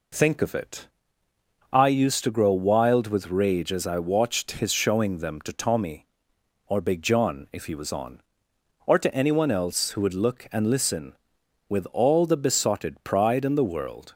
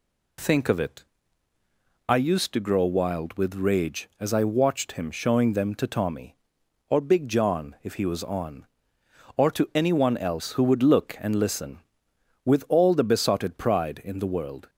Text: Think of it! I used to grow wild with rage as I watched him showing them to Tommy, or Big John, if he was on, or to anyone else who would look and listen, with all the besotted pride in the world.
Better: second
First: says "his" for "him"; at 4.6 s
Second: none

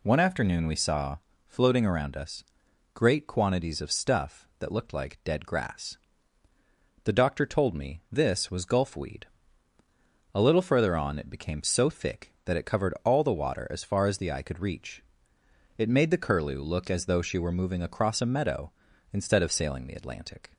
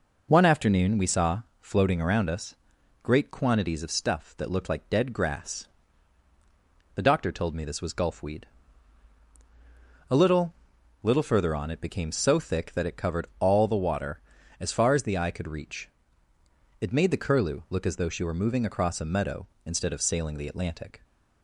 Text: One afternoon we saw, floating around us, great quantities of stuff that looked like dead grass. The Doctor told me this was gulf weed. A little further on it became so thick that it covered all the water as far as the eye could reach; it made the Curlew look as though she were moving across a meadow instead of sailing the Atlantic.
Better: first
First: none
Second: says "little" twice; at 11.0 s

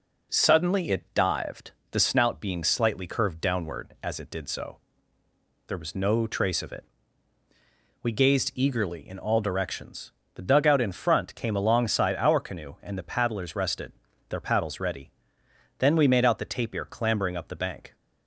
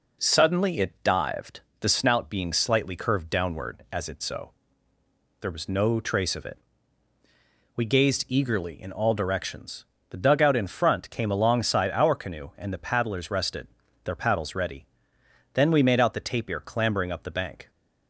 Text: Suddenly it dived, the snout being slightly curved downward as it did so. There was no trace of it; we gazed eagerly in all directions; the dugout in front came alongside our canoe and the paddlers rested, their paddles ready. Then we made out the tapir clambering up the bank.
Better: first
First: none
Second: skips "did"; at 4.2 s

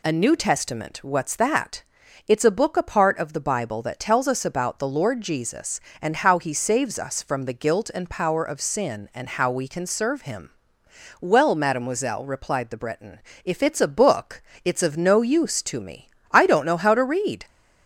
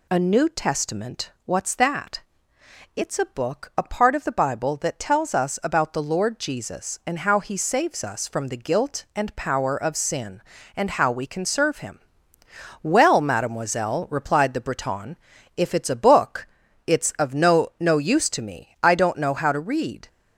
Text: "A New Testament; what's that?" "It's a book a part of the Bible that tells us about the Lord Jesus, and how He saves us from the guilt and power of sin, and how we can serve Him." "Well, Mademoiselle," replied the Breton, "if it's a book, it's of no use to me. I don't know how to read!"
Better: first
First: none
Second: says "no" twice; at 17.7 s

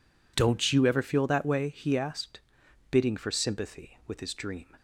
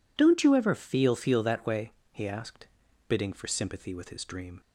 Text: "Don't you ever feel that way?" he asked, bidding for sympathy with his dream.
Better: first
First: none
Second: says "feel" twice; at 1.1 s

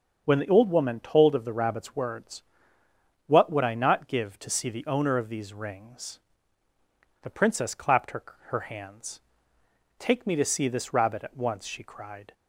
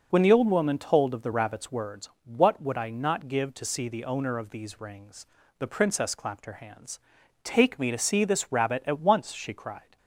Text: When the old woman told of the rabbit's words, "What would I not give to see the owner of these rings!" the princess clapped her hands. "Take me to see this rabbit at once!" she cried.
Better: second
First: starts louder than the rest; until 1.2 s; 6 dB // says "her" twice; at 8.4 s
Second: none

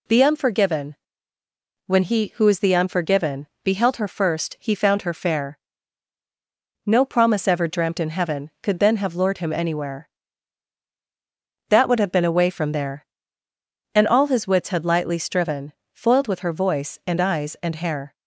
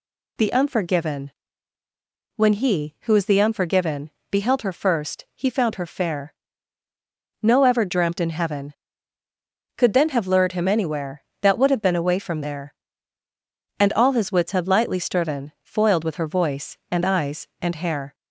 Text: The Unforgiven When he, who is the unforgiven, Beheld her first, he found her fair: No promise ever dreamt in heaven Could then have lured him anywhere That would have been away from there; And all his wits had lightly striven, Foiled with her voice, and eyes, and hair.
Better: first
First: pauses between "Unforgiven" and "When"; noticeable; at 0.9 s; 0.94 s long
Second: pauses between "Unforgiven" and "When"; at 1.3 s; 1.0 s long // skips "promise"; at 7.6 s

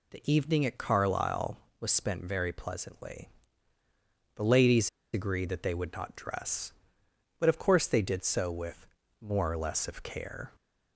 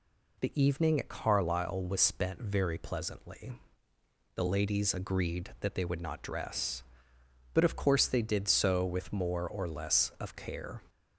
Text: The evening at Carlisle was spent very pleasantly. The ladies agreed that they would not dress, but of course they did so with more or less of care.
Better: second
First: pauses between "ladies" and "agreed"; slight; at 4.8 s; 0.25 s long // pauses between "with" and "more"; slight; at 8.8 s; 0.34 s long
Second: none

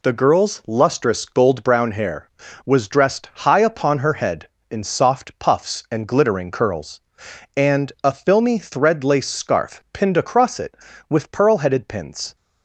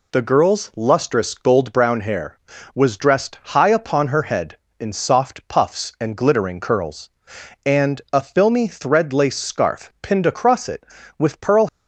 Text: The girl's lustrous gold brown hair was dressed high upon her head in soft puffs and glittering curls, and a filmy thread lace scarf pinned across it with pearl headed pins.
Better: first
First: none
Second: stops before "headed pins"; at 11.6 s

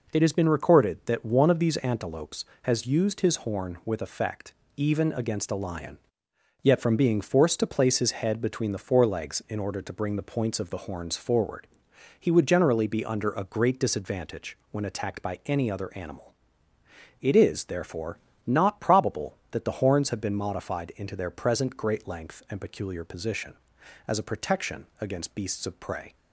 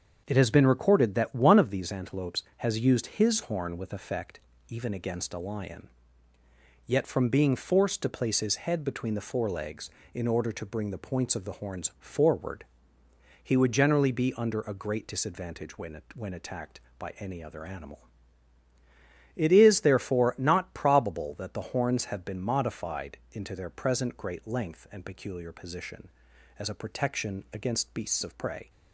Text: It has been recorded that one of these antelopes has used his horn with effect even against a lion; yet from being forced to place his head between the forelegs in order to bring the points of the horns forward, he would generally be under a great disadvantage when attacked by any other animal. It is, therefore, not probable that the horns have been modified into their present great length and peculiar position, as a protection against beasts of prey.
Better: first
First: pauses between "effect" and "even"; slight; at 4.5 s; 0.20 s long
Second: starts louder than the rest; until 1.2 s; 7 dB // pauses between "effect" and "even"; slight; at 4.3 s; 0.30 s long // says "when" twice; at 16.1 s // pauses between "modified" and "into"; slight; at 23.1 s; 0.16 s long

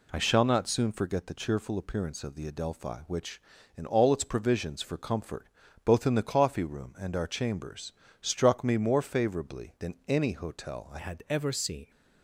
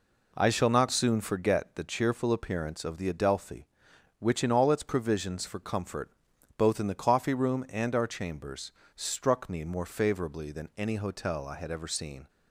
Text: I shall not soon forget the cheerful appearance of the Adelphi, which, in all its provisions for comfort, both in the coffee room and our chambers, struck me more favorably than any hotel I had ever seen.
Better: second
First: changes voice at "had"; from 10.9 s on; 1.0 s long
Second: none

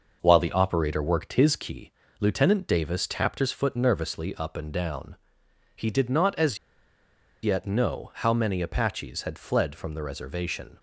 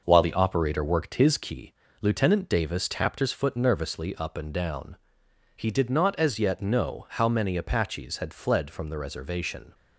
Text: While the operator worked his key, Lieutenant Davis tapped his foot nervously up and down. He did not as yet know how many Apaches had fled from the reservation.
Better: second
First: pauses between "as" and "yet"; noticeable; at 6.5 s; 0.85 s long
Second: none

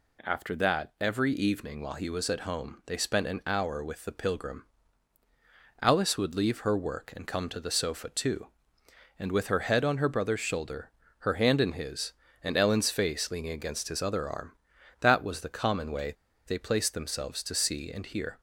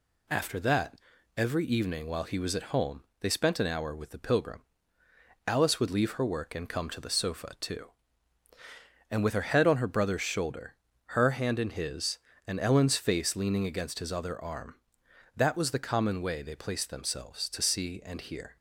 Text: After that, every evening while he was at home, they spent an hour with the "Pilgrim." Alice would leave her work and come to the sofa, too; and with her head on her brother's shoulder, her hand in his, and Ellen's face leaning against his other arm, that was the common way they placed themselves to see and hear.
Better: second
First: pauses between "way" and "they"; slight; at 16.1 s; 0.32 s long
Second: none

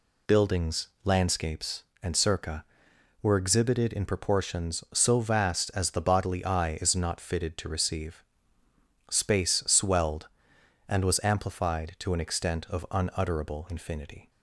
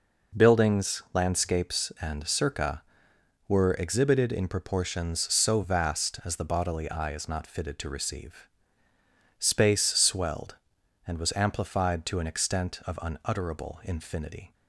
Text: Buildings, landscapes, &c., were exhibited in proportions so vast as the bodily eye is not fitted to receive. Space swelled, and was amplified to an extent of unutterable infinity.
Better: neither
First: none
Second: none

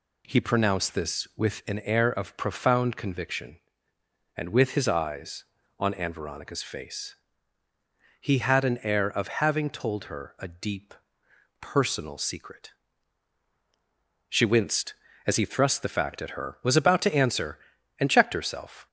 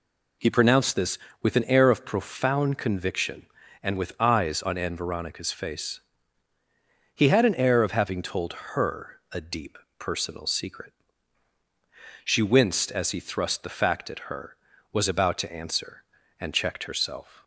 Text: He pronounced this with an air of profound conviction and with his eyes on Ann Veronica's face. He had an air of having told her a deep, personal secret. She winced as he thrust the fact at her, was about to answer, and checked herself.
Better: first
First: none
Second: skips "his"; at 4.1 s // pauses between "told" and "her"; slight; at 8.5 s; 0.18 s long

